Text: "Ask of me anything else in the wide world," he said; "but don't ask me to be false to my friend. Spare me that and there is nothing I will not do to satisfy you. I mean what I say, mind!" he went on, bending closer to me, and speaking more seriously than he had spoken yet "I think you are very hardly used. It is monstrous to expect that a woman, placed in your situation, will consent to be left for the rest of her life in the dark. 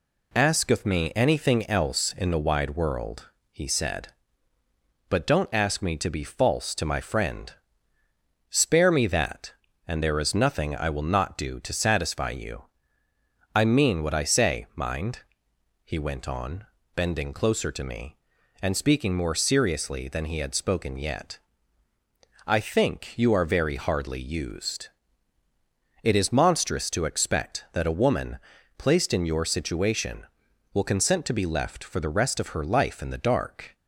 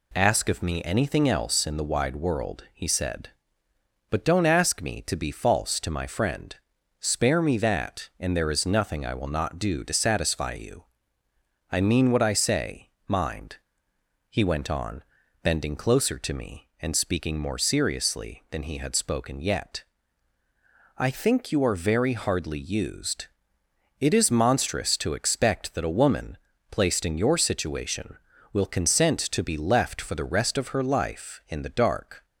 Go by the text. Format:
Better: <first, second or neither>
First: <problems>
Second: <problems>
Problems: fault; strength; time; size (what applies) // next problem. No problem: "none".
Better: neither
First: pauses between "yet" and "I"; at 21.4 s; 1.0 s long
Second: pauses between "yet" and "I"; at 19.8 s; 1.1 s long